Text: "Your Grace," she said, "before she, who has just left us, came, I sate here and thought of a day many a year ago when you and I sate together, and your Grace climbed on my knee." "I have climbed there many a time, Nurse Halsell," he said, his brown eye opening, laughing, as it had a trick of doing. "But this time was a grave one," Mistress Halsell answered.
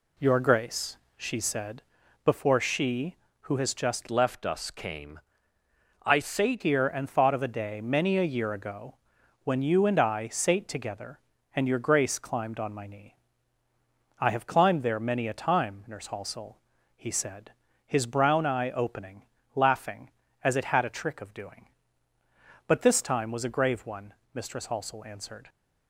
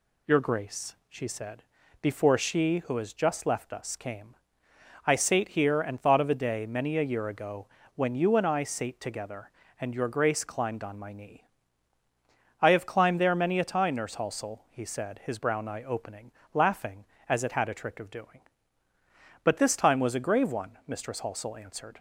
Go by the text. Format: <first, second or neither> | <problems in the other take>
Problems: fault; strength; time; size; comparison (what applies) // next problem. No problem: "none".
second | changes voice from "left" to "sate"; from 4.0 to 6.6 s; 2.6 s long // pauses between "ago" and "when"; noticeable; at 8.9 s; 0.48 s long; slight in the second